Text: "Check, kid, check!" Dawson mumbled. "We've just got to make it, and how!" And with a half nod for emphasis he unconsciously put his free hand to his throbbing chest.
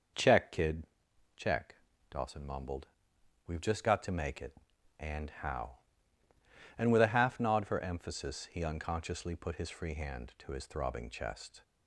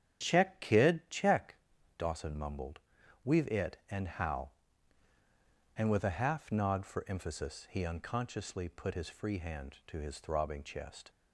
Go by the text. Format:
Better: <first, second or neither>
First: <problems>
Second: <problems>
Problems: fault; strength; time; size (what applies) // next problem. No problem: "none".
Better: first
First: none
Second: starts louder than the rest; strong; until 1.2 s; 8.5 dB // skips "just got to make"; at 3.4 s